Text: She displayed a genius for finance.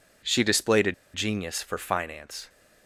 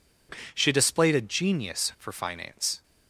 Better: second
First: pauses between "a" and "genius"; slight; at 0.9 s; 0.22 s long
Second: none

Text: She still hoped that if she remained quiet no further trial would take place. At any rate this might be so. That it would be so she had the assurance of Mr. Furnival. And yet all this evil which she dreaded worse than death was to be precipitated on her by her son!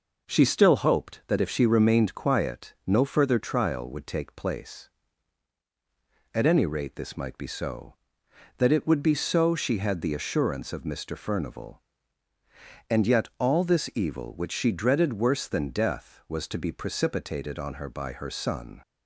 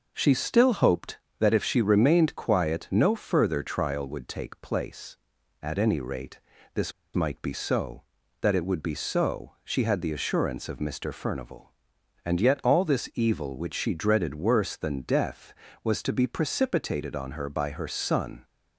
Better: first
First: none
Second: pauses between "rate" and "this"; slight; at 6.3 s; 0.36 s long // pauses between "this" and "might"; slight; at 6.9 s; 0.24 s long

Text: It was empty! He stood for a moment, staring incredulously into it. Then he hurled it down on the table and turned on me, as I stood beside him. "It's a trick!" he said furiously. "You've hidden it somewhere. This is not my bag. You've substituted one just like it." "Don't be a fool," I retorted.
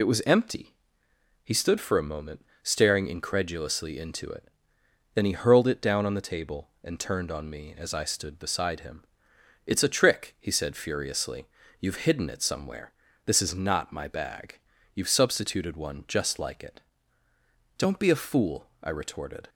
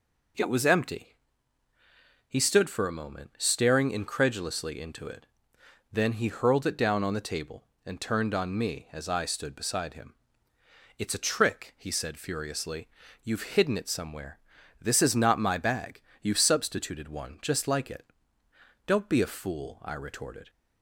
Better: second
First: loses the start of "It"; at 0.0 s; 35 ms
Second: none

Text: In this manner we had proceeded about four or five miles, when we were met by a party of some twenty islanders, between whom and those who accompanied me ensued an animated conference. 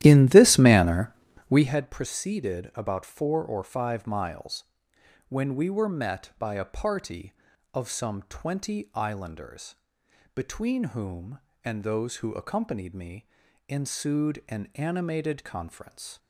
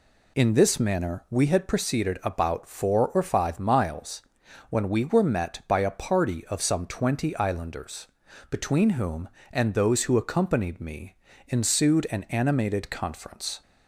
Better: second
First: starts louder than the rest; strong; until 1.8 s; 13.5 dB // pauses between "manner" and "we"; slight; at 1.1 s; 0.36 s long // pauses between "me" and "ensued"; at 13.2 s; 0.42 s long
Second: pauses between "me" and "ensued"; slight; at 11.1 s; 0.32 s long

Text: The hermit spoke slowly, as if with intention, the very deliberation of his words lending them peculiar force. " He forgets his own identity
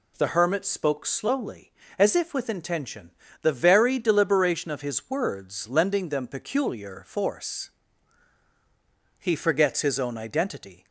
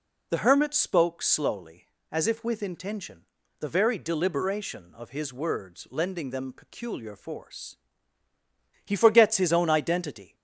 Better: neither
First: none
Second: none

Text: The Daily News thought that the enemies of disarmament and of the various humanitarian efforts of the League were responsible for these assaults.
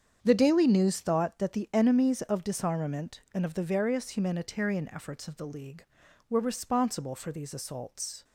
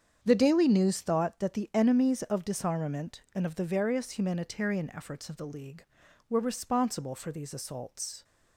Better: neither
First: starts louder than the rest; strong; until 1.2 s; 8 dB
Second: starts louder than the rest; strong; until 1.2 s; 8 dB

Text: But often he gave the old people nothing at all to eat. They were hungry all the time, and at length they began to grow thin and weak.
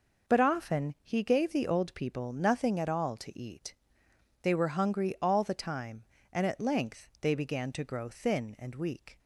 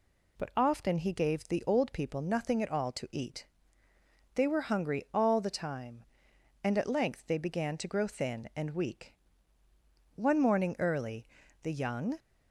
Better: first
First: none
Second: goes on to say "One morning early the young"; strong; from 10.1 s on; 2.0 s long

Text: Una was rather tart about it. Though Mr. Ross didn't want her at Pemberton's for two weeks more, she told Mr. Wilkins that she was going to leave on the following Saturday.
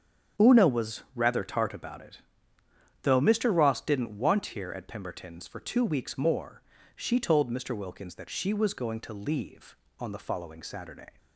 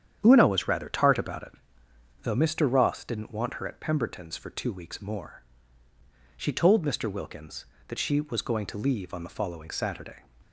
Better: second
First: starts louder than the rest; strong; until 1.5 s; 8 dB // says "here" for "her"; at 4.4 s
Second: starts louder than the rest; strong; until 1.2 s; 9 dB

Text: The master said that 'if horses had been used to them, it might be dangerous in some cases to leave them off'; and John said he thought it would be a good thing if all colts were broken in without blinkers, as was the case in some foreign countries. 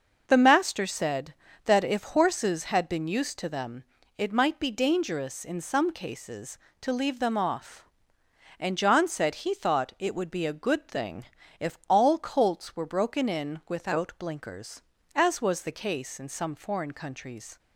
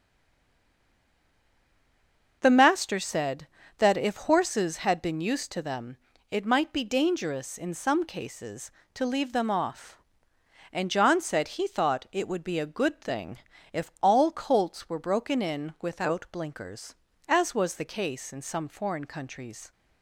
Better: first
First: pauses between "thing" and "if"; slight; at 11.2 s; 0.34 s long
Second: stays silent before the first word; until 2.4 s; 2.4 s long // pauses between "thing" and "if"; slight; at 13.3 s; 0.34 s long

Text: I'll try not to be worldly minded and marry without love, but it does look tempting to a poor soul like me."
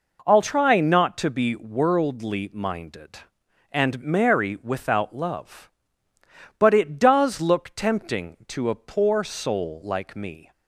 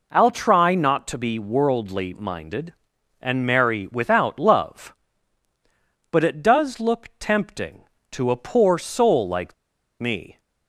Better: first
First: none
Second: pauses between "like" and "me"; noticeable; at 9.5 s; 0.46 s long

